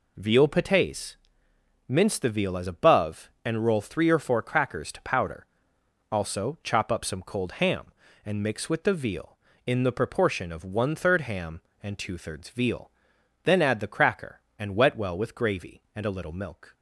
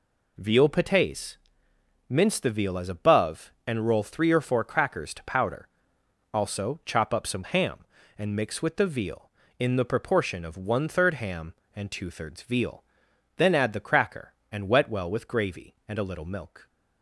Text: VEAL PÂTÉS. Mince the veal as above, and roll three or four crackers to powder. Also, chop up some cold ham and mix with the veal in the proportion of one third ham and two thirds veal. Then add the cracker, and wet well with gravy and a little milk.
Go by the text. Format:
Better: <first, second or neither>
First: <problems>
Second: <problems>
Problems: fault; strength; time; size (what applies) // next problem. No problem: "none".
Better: first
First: none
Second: skips "cold"; at 7.4 s